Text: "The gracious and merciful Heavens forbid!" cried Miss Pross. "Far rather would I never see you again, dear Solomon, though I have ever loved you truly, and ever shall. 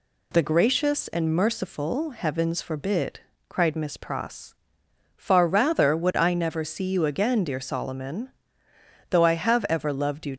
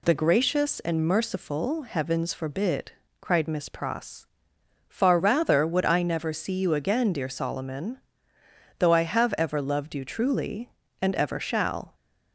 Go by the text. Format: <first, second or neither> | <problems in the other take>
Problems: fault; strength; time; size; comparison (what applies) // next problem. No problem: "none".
second | stops before "truly and ever shall"; at 10.3 s